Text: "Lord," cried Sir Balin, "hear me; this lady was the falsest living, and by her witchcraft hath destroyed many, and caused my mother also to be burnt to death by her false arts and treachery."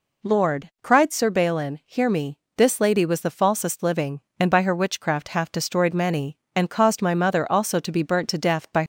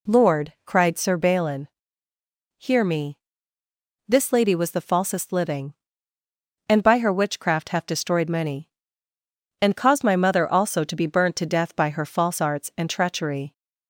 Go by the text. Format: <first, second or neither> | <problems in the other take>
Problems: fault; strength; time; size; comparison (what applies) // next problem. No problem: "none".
second | stops before "her false arts and treachery"; at 8.8 s